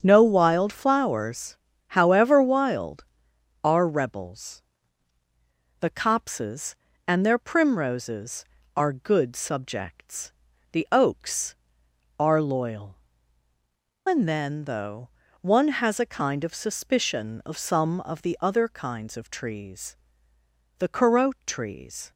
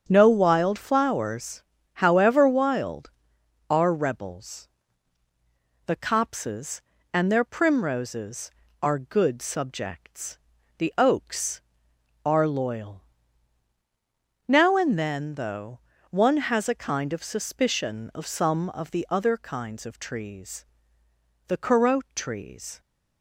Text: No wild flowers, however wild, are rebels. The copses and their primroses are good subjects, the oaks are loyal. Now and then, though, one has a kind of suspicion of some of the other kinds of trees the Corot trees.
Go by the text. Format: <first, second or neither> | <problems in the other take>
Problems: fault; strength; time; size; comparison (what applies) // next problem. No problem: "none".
second | starts louder than the rest; strong; until 1.0 s; 7.5 dB; strong in the second // skips "Now"; at 13.5 s // pauses between "trees" and "the"; noticeable; at 19.9 s; 0.82 s long; noticeable in the second